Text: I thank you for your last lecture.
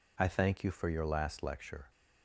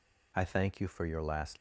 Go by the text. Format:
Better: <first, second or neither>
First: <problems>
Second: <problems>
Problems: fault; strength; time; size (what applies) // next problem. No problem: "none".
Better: first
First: none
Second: stops before "lecture"; at 1.5 s